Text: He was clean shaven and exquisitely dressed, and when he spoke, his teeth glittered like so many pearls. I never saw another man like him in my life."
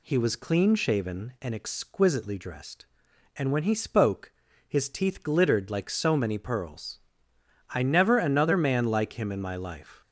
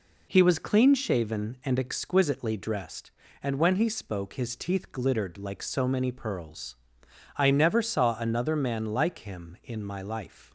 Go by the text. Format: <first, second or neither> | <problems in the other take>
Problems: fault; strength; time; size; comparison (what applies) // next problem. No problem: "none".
second | skips "saw"; at 8.1 s